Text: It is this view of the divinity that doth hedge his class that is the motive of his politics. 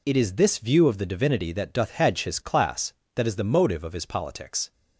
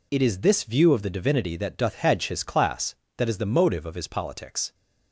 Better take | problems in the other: neither | none

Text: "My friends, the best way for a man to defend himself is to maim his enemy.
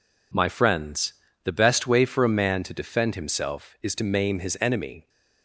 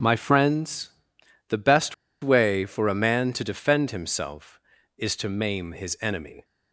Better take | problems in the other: first | starts louder than the rest; strong; until 1.6 s; 8 dB // pauses between "best" and "way"; slight; at 1.9 s; 0.27 s long

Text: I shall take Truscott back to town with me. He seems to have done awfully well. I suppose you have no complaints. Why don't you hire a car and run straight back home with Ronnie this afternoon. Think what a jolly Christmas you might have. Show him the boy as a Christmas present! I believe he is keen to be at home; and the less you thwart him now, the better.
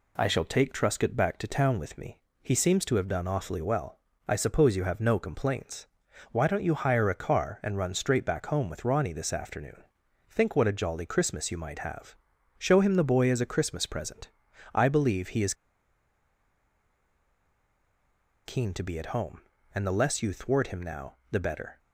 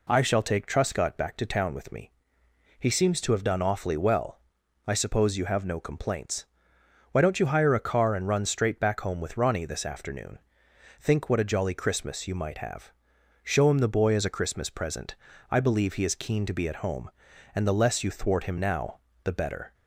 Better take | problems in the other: second | pauses between "is" and "keen"; strong; at 15.5 s; 2.9 s long

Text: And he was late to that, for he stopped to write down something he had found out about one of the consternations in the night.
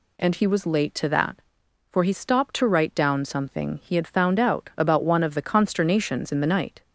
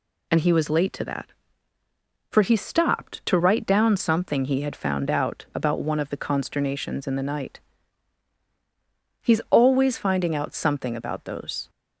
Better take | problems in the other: first | goes on to say "He's always finding out something about those"; strong; from 9.2 s on; 2.4 s long

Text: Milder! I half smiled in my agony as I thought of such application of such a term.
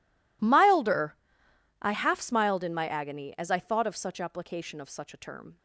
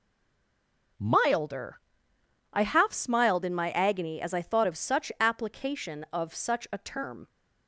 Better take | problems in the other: first | stays silent before the first word; until 0.9 s; 0.9 s long

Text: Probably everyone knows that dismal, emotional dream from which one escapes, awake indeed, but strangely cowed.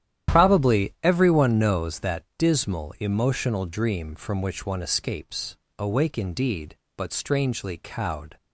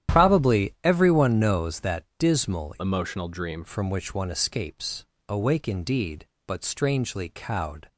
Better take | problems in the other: first | starts louder than the rest; strong; until 1.1 s; 11 dB; strong in the first // pauses between "that" and "dismal"; slight; at 2.0 s; 0.16 s long; slight in the first // changes voice from "emotional" to "dream"; from 2.8 to 3.6 s; 0.8 s long

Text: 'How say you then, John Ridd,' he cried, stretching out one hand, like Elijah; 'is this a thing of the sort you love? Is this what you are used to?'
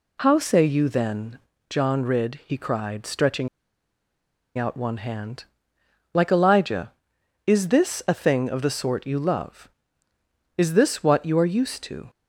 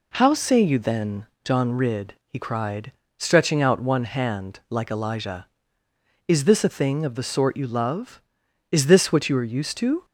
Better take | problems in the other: second | pauses between "stretching" and "out"; at 3.4 s; 1.0 s long

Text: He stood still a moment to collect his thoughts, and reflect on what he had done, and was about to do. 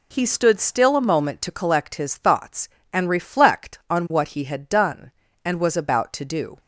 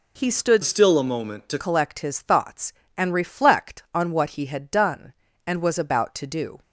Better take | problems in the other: first | changes voice from "still" to "to"; from 0.6 to 1.5 s; 0.9 s long

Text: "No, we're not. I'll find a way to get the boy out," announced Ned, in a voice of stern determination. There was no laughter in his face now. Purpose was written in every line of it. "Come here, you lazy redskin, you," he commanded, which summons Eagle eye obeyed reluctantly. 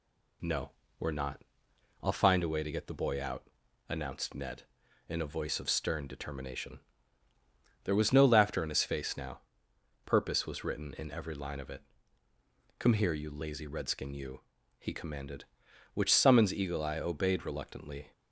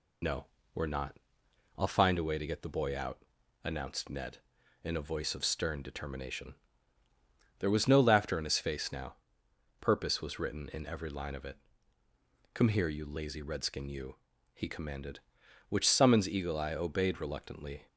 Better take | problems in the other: first | loses the start of "No"; at 0.2 s; 50 ms

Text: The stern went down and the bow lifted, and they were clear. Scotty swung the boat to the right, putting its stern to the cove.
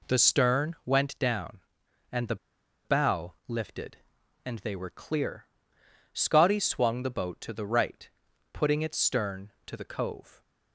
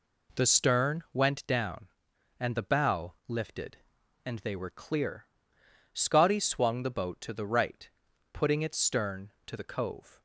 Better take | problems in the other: second | pauses between "the" and "bow"; noticeable; at 2.3 s; 0.49 s long

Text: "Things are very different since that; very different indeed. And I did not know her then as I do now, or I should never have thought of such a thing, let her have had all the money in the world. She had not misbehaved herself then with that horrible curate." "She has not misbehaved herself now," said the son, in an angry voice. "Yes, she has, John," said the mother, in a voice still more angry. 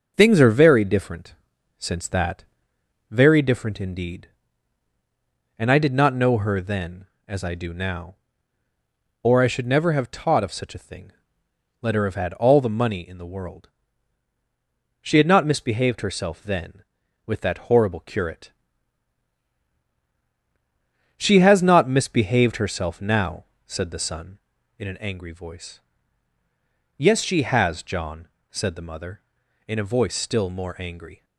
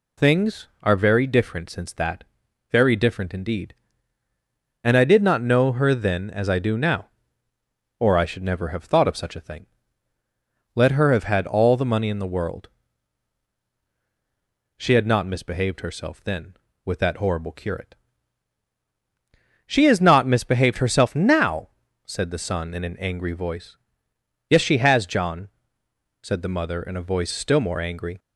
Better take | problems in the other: second | pauses between "different" and "since"; at 1.3 s; 0.44 s long // says "taught" for "thought"; at 10.1 s

